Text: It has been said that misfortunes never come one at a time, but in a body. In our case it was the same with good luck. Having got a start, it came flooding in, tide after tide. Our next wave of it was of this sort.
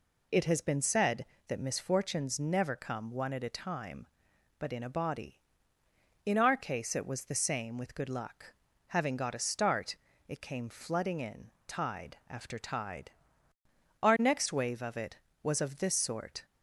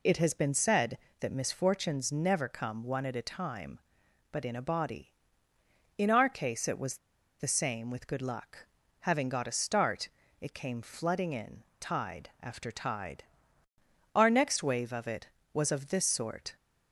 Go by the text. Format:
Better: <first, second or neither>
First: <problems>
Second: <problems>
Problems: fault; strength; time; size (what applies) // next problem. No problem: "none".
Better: first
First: none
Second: pauses between "was" and "the"; at 6.9 s; 0.42 s long